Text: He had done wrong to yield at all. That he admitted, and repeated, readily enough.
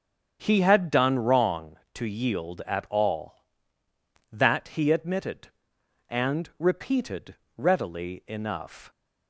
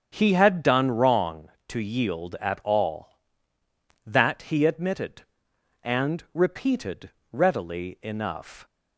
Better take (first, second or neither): neither